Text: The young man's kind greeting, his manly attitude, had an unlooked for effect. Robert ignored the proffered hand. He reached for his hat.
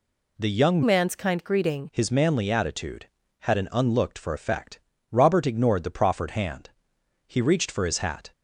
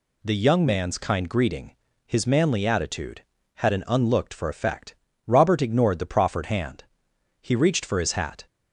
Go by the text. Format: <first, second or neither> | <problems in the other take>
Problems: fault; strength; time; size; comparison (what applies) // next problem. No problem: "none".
second | changes voice from "man's" to "greeting"; from 0.8 to 1.8 s; 1.0 s long